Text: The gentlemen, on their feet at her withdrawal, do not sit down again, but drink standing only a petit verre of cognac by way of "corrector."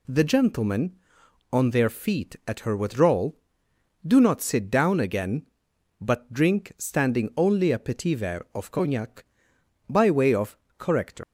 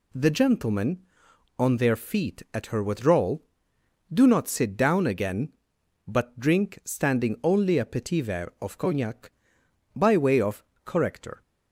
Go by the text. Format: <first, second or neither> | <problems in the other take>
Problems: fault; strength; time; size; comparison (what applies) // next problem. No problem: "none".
second | pauses between "of" and "corrector"; slight; at 10.5 s; 0.20 s long; slight in the second // leaves "corrector" unfinished; at 11.2 s; 115 ms